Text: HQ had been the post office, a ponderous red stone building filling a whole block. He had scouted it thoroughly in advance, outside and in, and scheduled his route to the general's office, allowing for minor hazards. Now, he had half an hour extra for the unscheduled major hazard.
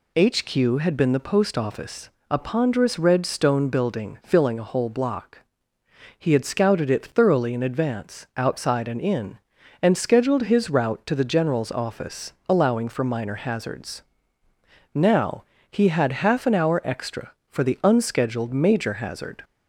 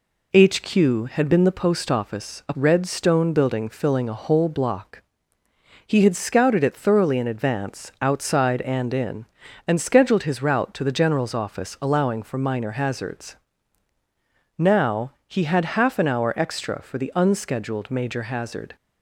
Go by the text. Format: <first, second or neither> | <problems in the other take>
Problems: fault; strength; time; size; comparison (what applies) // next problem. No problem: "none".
first | skips "ponderous"; at 2.5 s